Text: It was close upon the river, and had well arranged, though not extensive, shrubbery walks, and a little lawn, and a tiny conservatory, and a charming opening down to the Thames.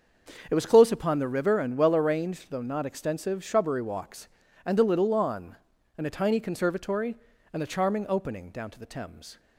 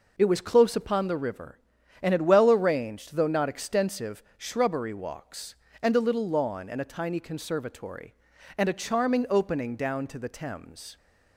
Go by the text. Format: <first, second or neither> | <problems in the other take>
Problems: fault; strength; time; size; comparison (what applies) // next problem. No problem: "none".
second | starts louder than the rest; until 1.5 s; 6.5 dB // skips "had"; at 1.7 s